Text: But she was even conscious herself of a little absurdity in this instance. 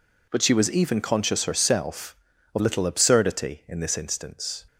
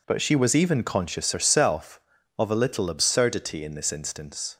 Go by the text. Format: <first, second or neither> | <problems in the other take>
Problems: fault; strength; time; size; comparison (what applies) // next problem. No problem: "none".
second | skips "a"; at 2.5 s